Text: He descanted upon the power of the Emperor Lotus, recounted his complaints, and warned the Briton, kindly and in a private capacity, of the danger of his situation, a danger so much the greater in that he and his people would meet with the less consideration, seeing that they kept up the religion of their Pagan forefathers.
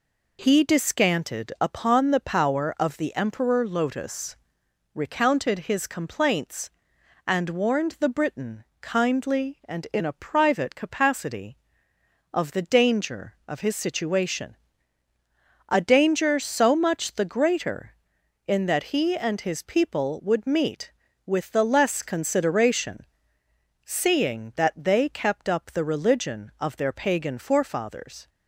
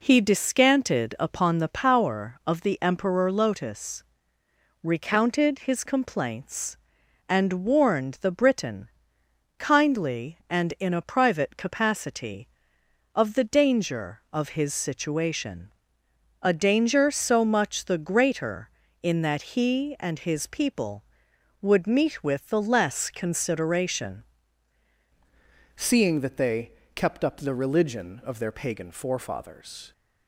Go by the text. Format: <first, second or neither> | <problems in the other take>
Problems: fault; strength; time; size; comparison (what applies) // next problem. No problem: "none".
first | changes voice at "seeing"; from 25.7 s on; 4.2 s long // pauses between "they" and "kept"; slight; at 26.6 s; 0.26 s long